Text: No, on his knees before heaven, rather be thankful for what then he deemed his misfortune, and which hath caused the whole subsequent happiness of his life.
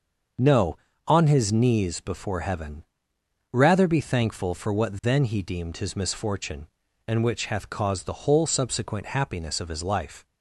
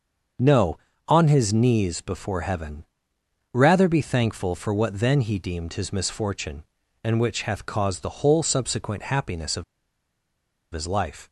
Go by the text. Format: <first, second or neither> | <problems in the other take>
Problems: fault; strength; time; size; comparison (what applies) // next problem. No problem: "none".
first | starts louder than the rest; until 1.6 s; 6.5 dB; also in the first // pauses between "of" and "his"; at 9.6 s; 1.0 s long